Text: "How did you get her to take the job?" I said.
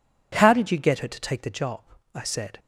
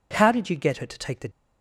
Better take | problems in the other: first | stops before "job I said"; at 1.2 s

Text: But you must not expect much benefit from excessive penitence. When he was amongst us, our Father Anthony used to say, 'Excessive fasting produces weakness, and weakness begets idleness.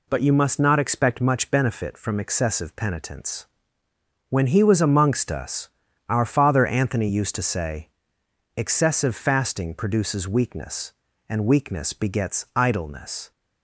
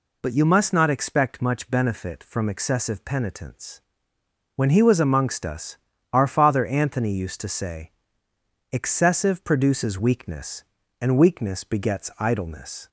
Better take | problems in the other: first | skips "fasting"; at 9.4 s

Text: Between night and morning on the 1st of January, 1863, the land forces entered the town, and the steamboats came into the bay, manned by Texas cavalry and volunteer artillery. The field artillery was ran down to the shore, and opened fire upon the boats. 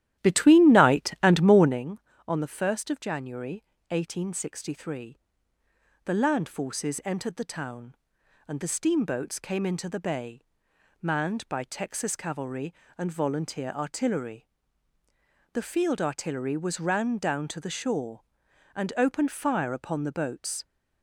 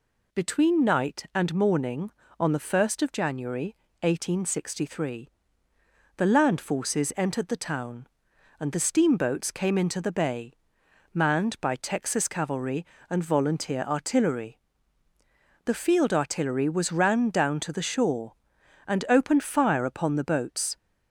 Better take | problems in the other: second | starts louder than the rest; strong; until 1.9 s; 13 dB

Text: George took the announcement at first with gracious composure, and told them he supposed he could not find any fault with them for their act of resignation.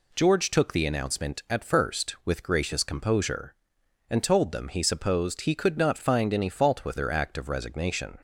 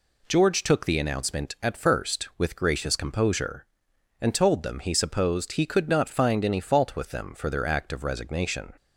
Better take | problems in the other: second | skips "them for"; at 6.9 s

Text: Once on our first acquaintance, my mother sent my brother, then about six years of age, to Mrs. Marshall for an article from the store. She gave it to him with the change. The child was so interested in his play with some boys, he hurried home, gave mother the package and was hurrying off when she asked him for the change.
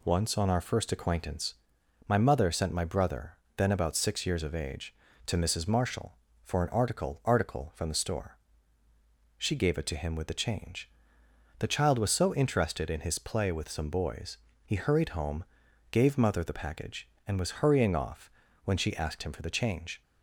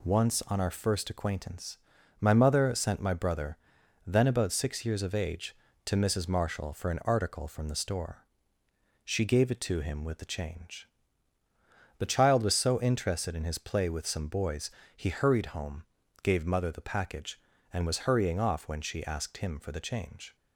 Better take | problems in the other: second | says "article" twice; at 7.2 s // pauses between "off" and "when"; slight; at 18.3 s; 0.34 s long

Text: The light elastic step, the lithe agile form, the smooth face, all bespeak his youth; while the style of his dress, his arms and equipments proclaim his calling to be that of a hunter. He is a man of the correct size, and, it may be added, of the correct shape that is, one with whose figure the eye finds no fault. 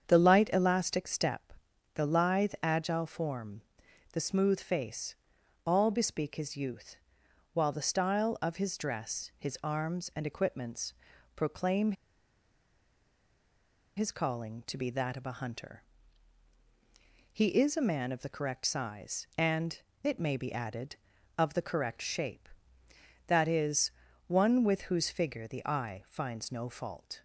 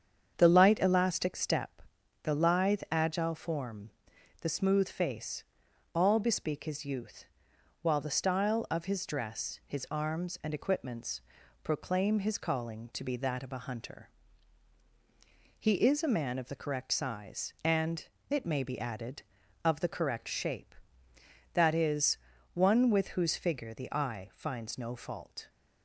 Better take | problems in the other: second | starts louder than the rest; strong; until 1.0 s; 7.5 dB; strong in the second // pauses between "equipments" and "proclaim"; at 10.9 s; 0.42 s long; also in the second // pauses between "proclaim" and "his"; strong; at 11.9 s; 2.0 s long

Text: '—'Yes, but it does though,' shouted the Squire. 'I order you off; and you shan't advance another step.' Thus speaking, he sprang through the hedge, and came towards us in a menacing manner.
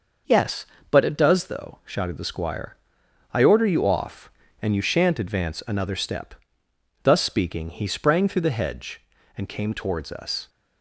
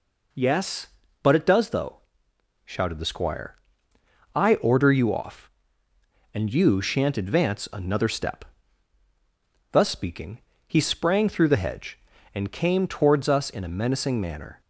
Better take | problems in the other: second | starts louder than the rest; noticeable; until 1.5 s; 6 dB // stops before "in a menacing manner"; at 10.4 s

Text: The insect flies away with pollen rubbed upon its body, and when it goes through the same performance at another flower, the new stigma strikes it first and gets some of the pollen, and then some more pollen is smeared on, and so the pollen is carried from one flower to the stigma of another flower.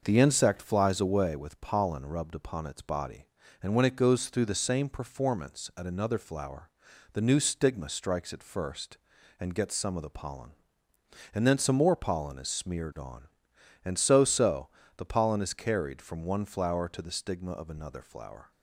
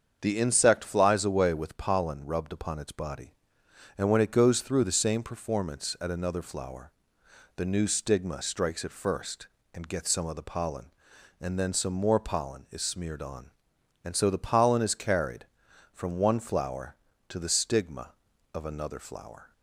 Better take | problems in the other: second | starts louder than the rest; noticeable; until 1.0 s; 6 dB; strong in the second // says "so" twice; at 14.2 s

